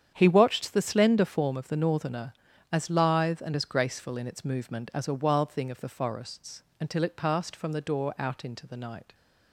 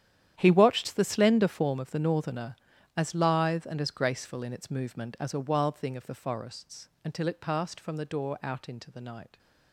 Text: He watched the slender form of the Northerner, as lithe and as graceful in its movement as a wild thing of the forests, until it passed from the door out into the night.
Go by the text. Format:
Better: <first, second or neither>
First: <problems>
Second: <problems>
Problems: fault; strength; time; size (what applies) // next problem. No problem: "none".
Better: first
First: starts louder than the rest; strong; until 1.1 s; 8.5 dB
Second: gets quieter; strong; throughout; 15.5 dB // starts louder than the rest; strong; until 1.3 s; 10.5 dB